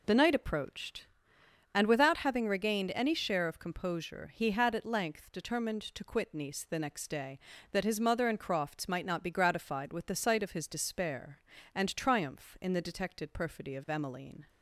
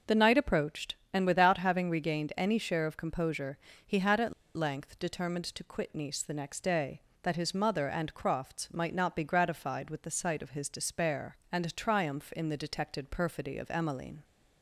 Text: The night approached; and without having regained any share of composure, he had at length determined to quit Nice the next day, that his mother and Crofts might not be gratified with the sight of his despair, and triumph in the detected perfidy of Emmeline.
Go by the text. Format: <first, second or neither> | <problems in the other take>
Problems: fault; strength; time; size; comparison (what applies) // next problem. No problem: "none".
first | pauses between "at" and "length"; slight; at 4.3 s; 0.24 s long